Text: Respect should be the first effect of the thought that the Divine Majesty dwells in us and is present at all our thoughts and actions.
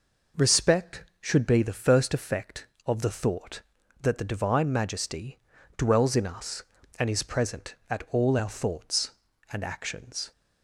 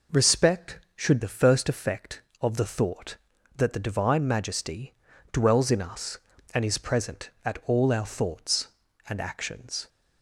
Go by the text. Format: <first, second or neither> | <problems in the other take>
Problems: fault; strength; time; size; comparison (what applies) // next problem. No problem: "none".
first | skips "be"; at 1.2 s // pauses between "Majesty" and "dwells"; at 4.9 s; 0.38 s long; also in the first